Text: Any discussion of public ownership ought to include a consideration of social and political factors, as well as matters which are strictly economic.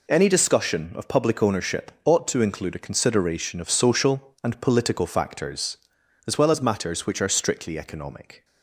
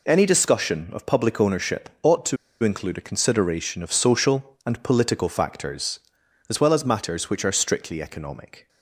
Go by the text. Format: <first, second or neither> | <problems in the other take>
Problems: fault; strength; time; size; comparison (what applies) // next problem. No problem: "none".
first | pauses between "to" and "include"; slight; at 2.3 s; 0.25 s long